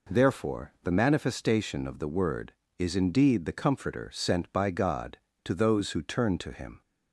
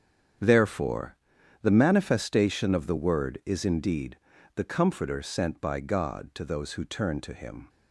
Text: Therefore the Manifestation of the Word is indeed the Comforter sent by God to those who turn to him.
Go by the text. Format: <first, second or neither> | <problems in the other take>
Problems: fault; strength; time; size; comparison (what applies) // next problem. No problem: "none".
first | gets quieter; strong; throughout; 12 dB // pauses between "Therefore" and "the"; noticeable; at 1.1 s; 0.46 s long // pauses between "indeed" and "the"; at 4.1 s; 0.38 s long